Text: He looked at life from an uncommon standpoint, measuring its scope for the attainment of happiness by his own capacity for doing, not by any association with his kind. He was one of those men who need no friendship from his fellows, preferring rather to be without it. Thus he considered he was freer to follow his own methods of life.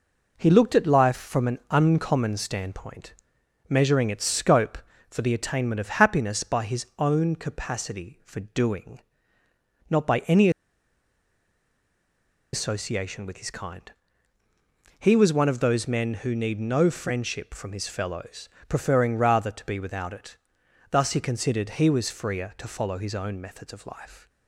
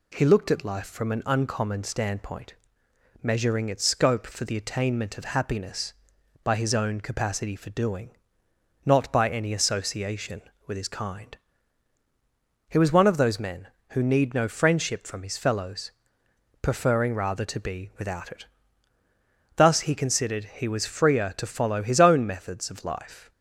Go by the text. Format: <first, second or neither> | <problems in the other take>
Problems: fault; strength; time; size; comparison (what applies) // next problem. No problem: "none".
second | pauses between "any" and "association"; strong; at 10.4 s; 2.0 s long